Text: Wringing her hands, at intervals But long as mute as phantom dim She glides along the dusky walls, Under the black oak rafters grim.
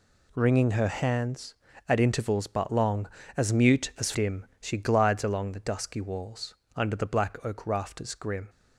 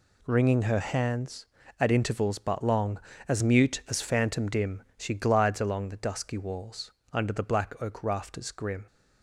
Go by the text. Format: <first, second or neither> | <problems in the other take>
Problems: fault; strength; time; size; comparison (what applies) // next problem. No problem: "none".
second | skips "phantom"; at 4.1 s // pauses between "dim" and "She"; slight; at 4.4 s; 0.16 s long; slight in the second